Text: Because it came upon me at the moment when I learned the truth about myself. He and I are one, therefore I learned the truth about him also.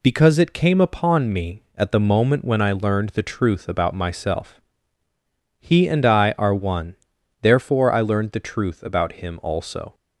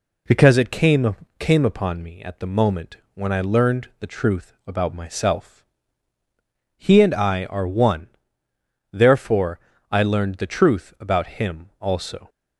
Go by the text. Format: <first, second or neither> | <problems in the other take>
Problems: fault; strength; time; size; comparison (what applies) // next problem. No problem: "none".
first | says "came" twice; at 1.3 s // pauses between "moment" and "when"; slight; at 2.9 s; 0.18 s long // pauses between "therefore" and "I"; slight; at 9.5 s; 0.30 s long